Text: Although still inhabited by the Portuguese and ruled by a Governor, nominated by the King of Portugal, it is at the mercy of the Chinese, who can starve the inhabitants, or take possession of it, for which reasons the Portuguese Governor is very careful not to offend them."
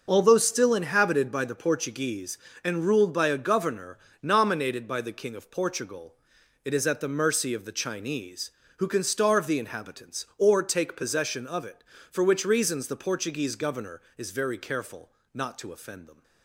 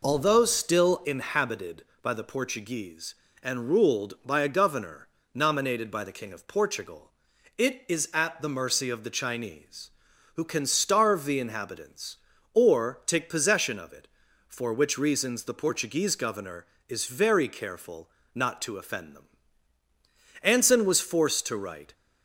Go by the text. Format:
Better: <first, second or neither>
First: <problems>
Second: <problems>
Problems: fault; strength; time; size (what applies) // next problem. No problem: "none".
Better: first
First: pauses between "careful" and "not"; slight; at 15.1 s; 0.24 s long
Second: pauses between "careful" and "not"; slight; at 18.0 s; 0.26 s long // goes on to say "Anson was forced to write"; from 20.4 s on; 1.5 s long